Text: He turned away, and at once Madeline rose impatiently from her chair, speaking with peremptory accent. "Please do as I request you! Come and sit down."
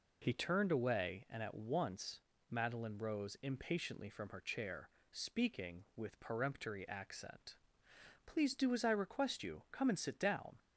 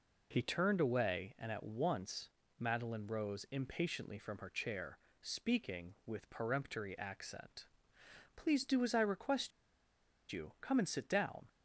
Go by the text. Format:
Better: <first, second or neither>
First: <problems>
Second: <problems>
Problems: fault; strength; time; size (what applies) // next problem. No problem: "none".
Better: first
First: pauses between "once" and "Madeline"; slight; at 2.2 s; 0.28 s long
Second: pauses between "once" and "Madeline"; slight; at 2.2 s; 0.28 s long // pauses between "request" and "you"; noticeable; at 9.5 s; 0.81 s long